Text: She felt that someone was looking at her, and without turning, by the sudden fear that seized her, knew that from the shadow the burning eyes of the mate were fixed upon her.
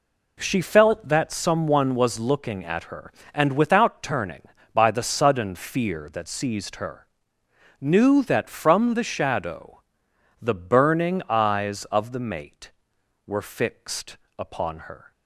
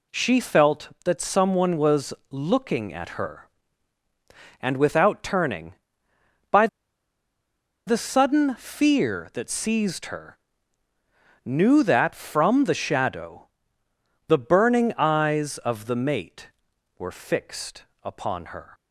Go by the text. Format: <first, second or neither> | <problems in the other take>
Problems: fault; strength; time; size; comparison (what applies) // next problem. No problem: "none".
first | pauses between "was" and "looking"; slight; at 2.1 s; 0.18 s long // pauses between "by" and "the"; at 6.6 s; 1.2 s long // pauses between "shadow" and "the"; noticeable; at 13.4 s; 0.80 s long; noticeable in the first // pauses between "fixed" and "upon"; slight; at 17.8 s; 0.20 s long; slight in the first